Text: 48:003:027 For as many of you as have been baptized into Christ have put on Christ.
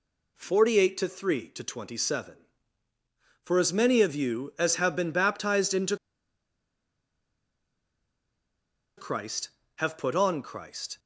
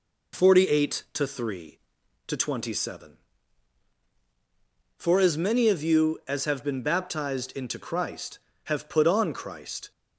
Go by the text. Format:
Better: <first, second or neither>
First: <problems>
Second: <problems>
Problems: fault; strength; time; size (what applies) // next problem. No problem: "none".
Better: second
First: pauses between "into" and "Christ"; strong; at 5.9 s; 3.0 s long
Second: none